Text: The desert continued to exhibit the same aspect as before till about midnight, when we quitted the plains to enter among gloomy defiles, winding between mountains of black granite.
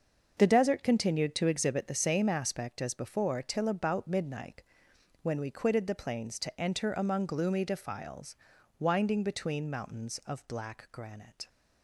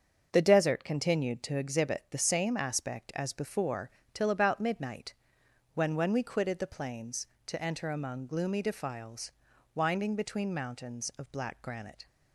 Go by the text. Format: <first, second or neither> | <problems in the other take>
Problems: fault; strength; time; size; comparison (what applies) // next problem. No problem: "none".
first | starts louder than the rest; until 1.3 s; 6.5 dB; also in the first // pauses between "before" and "till"; slight; at 3.9 s; 0.22 s long // says "when" twice; at 5.9 s